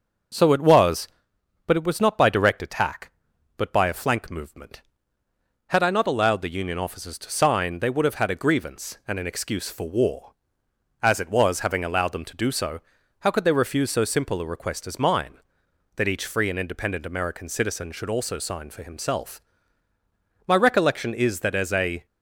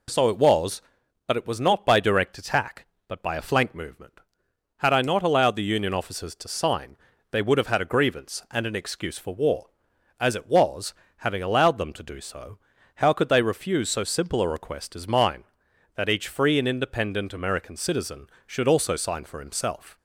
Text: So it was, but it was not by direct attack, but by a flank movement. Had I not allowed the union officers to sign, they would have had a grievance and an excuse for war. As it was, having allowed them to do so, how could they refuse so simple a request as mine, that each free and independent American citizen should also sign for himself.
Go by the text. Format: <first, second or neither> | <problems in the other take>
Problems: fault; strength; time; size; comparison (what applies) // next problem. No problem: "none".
second | starts louder than the rest; until 1.9 s; 6 dB // goes on to say "My recollection is that as a"; from 20.4 s on; 1.5 s long